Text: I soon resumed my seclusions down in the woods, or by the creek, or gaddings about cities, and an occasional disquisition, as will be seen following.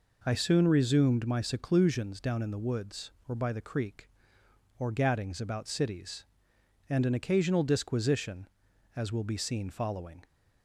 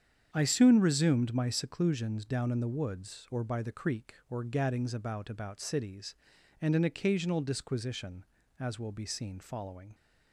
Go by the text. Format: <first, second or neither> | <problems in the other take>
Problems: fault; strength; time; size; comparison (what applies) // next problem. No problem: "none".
first | starts louder than the rest; strong; until 1.3 s; 8 dB // says "about" twice; at 5.3 s